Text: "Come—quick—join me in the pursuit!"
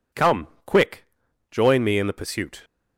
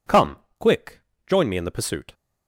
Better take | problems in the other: neither | none

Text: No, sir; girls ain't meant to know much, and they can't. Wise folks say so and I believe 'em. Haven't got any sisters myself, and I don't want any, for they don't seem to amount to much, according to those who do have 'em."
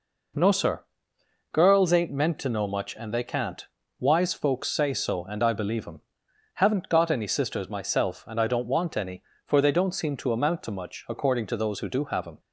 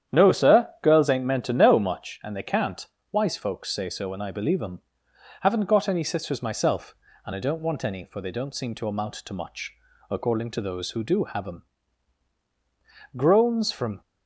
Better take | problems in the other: first | starts louder than the rest; strong; until 1.2 s; 9.5 dB // goes on to say "Groans from"; noticeable; from 13.1 s on; 0.84 s long

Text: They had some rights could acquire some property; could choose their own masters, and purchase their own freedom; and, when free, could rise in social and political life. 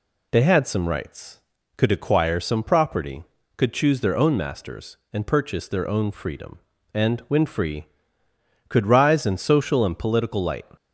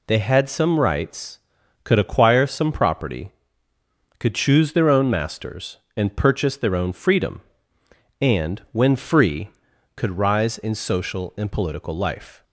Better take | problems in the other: second | says "light" for "life"; at 10.4 s

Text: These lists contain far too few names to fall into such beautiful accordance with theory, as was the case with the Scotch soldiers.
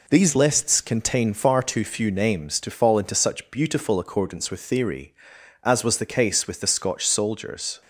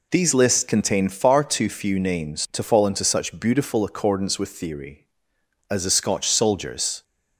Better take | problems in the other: first | skips "was the case with"; at 5.8 s

